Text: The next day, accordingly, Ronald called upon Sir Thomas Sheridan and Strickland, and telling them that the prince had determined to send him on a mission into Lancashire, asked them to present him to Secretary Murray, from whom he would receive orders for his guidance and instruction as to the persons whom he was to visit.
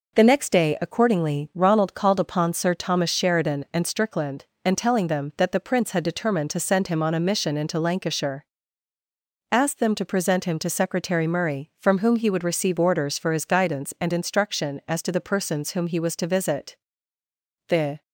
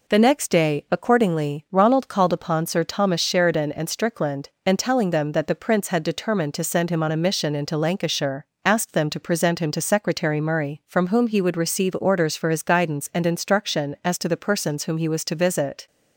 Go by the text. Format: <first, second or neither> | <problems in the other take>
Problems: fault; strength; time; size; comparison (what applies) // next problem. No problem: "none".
second | goes on to say "The"; slight; from 17.6 s on; 0.32 s long